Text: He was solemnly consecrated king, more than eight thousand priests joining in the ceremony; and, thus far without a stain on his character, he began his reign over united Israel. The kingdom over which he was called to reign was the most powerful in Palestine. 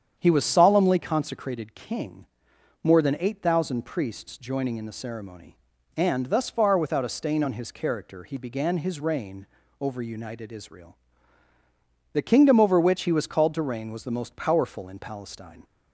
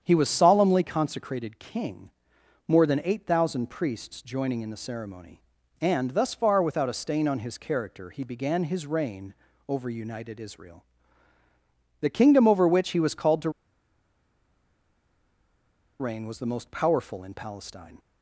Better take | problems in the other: first | starts louder than the rest; strong; until 1.0 s; 8 dB; strong in the first // pauses between "reign" and "over"; slight; at 9.3 s; 0.34 s long; slight in the first // pauses between "to" and "reign"; strong; at 13.4 s; 2.5 s long

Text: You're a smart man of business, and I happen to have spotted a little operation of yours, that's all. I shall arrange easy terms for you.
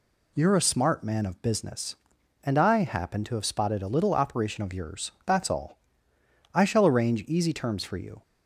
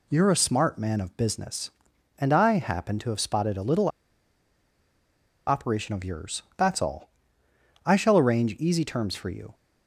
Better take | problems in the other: first | pauses between "little" and "operation"; strong; at 3.8 s; 1.5 s long

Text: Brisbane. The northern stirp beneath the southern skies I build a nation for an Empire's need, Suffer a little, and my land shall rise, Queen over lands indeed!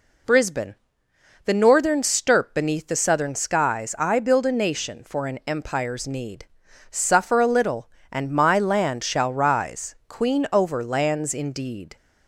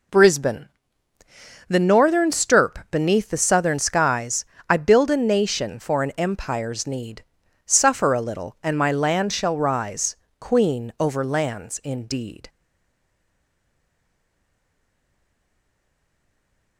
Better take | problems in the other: first | pauses between "skies" and "I"; slight; at 4.4 s; 0.24 s long // stays silent after the last word; strong; from 12.4 s on; 4.3 s long

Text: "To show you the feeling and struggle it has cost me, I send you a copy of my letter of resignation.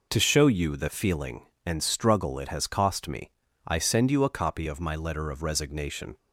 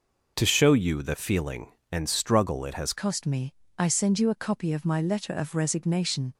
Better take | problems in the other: first | changes voice at "cost"; from 2.9 s on; 3.4 s long

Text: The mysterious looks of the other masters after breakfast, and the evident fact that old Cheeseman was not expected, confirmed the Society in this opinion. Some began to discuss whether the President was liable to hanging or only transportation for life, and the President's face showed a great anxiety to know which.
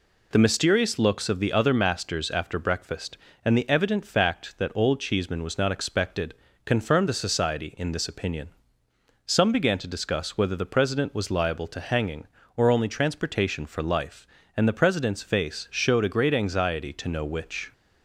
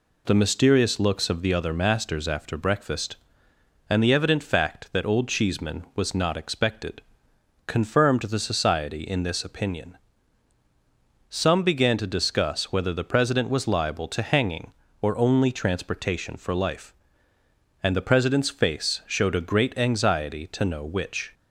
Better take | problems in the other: neither | none

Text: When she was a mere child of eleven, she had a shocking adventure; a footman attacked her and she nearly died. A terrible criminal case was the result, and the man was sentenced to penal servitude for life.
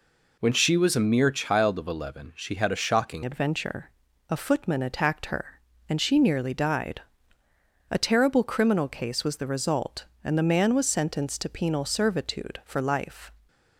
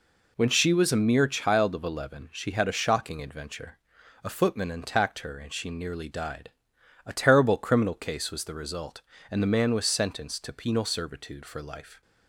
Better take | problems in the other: second | changes voice at "adventure"; from 3.2 s on; 10.1 s long

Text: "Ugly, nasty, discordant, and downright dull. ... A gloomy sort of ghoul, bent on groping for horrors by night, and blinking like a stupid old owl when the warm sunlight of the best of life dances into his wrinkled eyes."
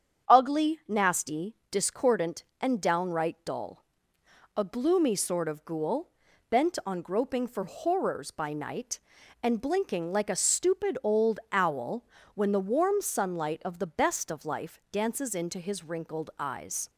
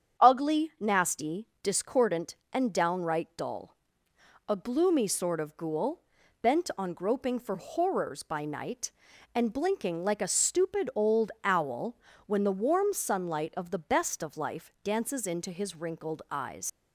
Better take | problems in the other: first | starts louder than the rest; strong; until 1.3 s; 8 dB; strong in the first // pauses between "owl" and "when"; slight; at 11.9 s; 0.30 s long; slight in the first // leaves "eyes" unfinished; at 16.6 s; 115 ms

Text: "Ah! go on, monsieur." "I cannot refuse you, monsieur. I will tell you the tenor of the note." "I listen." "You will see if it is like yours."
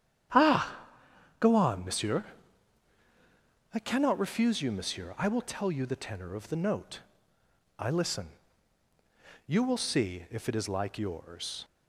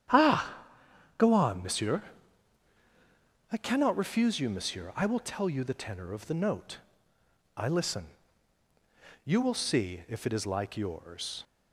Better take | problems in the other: neither | starts louder than the rest; strong; the same in both

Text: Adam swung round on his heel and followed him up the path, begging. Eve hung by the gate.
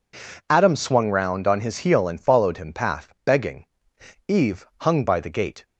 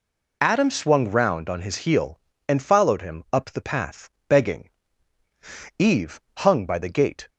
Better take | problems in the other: second | skips "up the"; at 2.7 s // pauses between "Eve" and "hung"; slight; at 4.6 s; 0.18 s long; slight in the second

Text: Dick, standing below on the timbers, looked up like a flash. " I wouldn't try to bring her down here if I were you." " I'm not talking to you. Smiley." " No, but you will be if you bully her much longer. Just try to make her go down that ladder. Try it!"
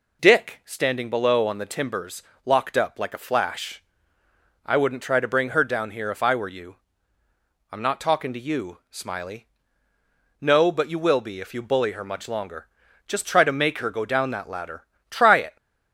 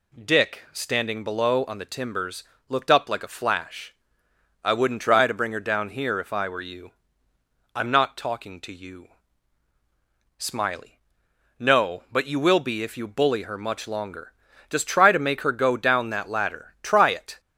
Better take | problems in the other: second | says "locked" for "looked"; at 2.4 s

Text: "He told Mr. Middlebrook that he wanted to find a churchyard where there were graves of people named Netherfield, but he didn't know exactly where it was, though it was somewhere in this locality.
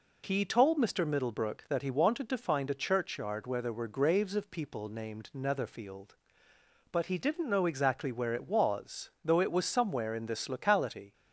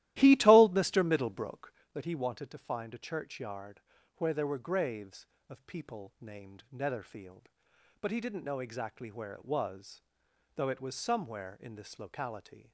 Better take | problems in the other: first | starts louder than the rest; strong; until 1.8 s; 14.5 dB // pauses between "churchyard" and "where"; slight; at 3.8 s; 0.34 s long

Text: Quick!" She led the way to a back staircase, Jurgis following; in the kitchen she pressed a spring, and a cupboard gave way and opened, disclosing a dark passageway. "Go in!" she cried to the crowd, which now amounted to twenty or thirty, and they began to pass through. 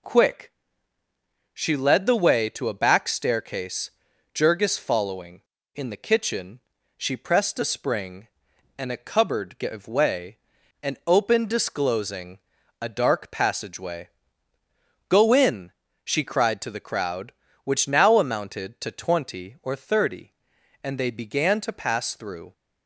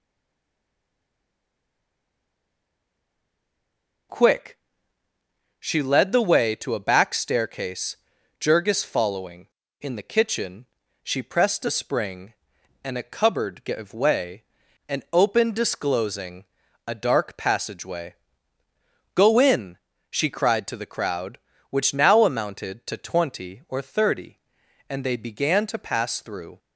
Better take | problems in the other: first | stays silent before the first word; strong; until 4.1 s; 4.1 s long // pauses between "kitchen" and "she"; at 10.6 s; 0.38 s long; also in the first // pauses between "disclosing" and "a"; at 16.4 s; 0.44 s long; also in the first

